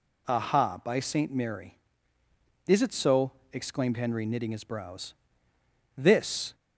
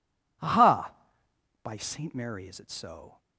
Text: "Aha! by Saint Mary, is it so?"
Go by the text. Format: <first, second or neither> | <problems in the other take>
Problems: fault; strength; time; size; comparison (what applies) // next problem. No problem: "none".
second | goes on to say "exclaimed Henry knitting his brows This"; strong; from 3.5 s on; 3.0 s long